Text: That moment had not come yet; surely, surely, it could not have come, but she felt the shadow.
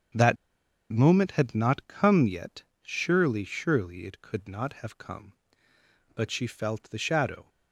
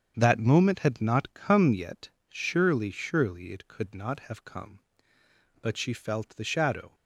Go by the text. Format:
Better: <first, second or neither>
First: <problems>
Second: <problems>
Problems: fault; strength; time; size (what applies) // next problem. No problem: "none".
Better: second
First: starts louder than the rest; strong; until 1.7 s; 8 dB // pauses between "That" and "moment"; noticeable; at 0.3 s; 0.56 s long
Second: starts louder than the rest; strong; until 1.1 s; 7.5 dB